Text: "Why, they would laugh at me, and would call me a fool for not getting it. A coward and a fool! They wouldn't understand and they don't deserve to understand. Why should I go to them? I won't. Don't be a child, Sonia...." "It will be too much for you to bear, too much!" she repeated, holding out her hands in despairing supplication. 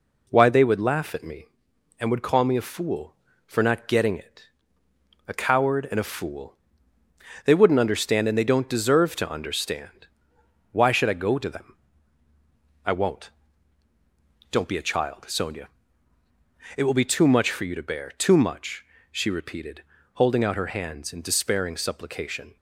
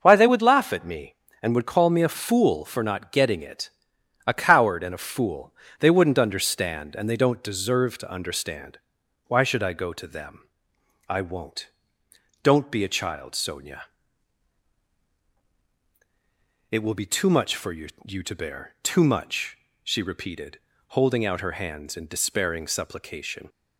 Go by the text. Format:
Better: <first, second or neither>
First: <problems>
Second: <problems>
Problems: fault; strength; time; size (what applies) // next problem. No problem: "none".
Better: first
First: none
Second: starts louder than the rest; until 1.0 s; 6.5 dB // says "you" twice; at 18.0 s